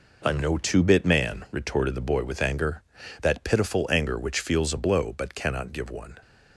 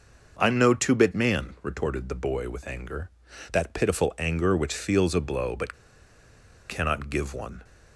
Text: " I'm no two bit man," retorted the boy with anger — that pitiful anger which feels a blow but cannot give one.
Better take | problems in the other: first | pauses between "but" and "cannot"; noticeable; at 5.7 s; 0.96 s long

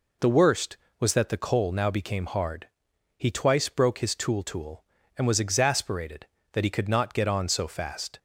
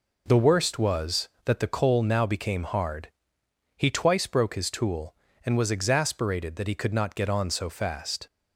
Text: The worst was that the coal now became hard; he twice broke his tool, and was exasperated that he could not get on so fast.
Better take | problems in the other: second | says "tool" twice; at 4.4 s

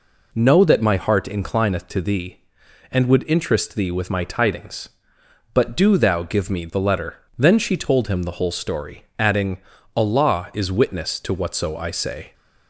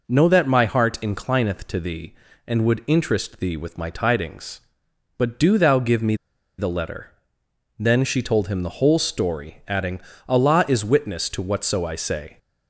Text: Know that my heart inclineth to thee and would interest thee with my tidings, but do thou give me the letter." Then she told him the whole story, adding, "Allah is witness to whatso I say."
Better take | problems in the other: first | pauses between "me" and "the"; at 6.1 s; 0.43 s long

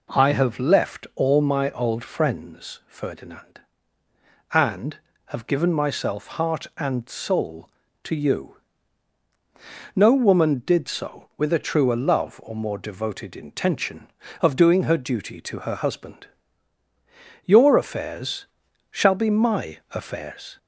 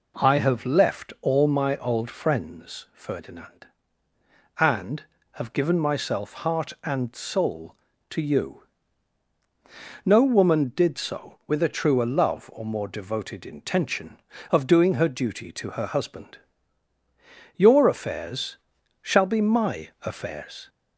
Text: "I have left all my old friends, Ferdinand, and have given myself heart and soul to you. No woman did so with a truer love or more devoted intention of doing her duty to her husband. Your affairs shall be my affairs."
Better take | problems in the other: neither | pauses between "affairs" and "shall"; the same in both

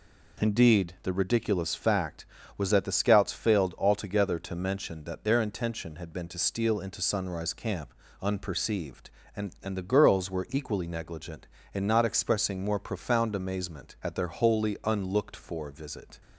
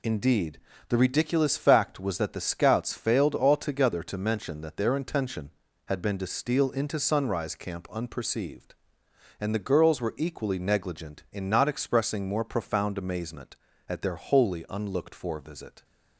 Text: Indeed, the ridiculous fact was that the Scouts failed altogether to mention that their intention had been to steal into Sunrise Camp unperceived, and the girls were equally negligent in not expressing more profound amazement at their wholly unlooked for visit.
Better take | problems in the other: second | pauses between "Camp" and "unperceived"; slight; at 7.9 s; 0.30 s long // says "and" twice; at 9.6 s

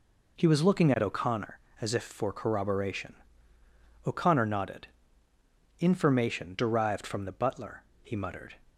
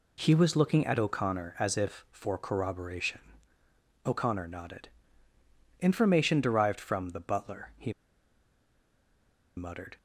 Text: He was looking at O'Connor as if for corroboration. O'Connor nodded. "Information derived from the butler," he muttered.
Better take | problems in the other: first | pauses between "he" and "muttered"; strong; at 7.9 s; 1.6 s long

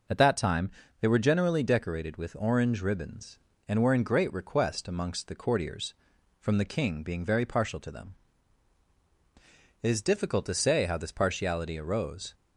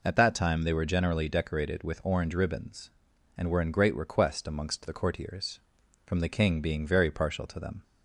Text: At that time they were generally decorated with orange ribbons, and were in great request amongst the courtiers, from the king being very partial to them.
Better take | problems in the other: second | pauses between "time" and "they"; slight; at 0.6 s; 0.30 s long // goes on to say "It is difficult to say how this partiality arose"; strong; from 9.8 s on; 2.5 s long

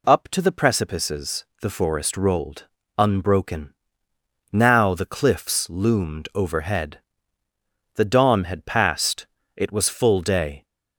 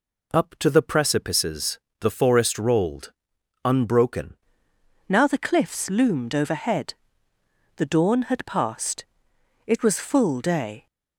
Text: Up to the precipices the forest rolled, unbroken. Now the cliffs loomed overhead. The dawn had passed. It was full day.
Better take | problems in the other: first | pauses between "precipices" and "the"; slight; at 1.7 s; 0.22 s long; slight in the first // changes voice at "Now"; from 5.0 s on; 5.8 s long

